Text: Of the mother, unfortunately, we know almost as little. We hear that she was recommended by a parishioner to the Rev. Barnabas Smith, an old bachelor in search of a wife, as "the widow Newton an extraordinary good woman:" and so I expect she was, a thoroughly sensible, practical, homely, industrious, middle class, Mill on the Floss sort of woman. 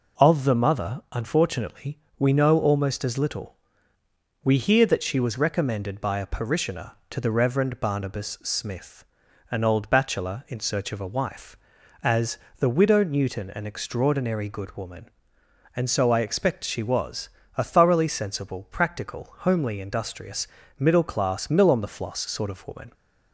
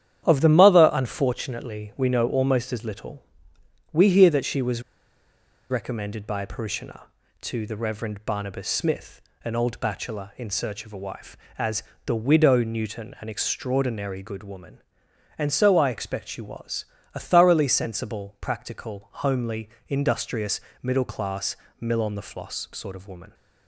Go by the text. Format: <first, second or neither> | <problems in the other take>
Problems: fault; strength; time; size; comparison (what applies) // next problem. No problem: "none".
first | starts louder than the rest; strong; until 1.2 s; 10 dB // pauses between "was" and "recommended"; noticeable; at 4.8 s; 0.90 s long // pauses between "as" and "the"; slight; at 11.8 s; 0.22 s long; slight in the first